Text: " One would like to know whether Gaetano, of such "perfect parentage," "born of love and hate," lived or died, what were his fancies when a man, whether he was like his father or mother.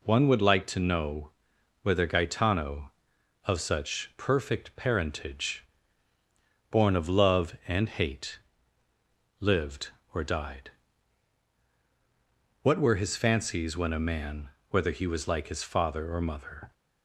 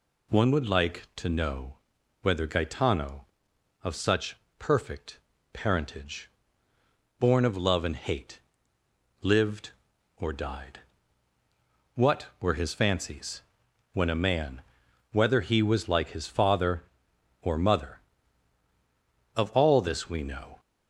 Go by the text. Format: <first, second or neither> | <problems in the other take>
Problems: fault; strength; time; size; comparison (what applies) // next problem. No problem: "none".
first | pauses between "know" and "whether"; at 1.7 s; 0.42 s long; noticeable in the first // pauses between "such" and "perfect"; slight; at 4.3 s; 0.24 s long // pauses between "perfect" and "parentage"; slight; at 5.1 s; 0.36 s long // pauses between "fancies" and "when"; noticeable; at 13.4 s; 0.52 s long // goes on to say "Of all this we know"; noticeable; from 19.3 s on; 1.2 s long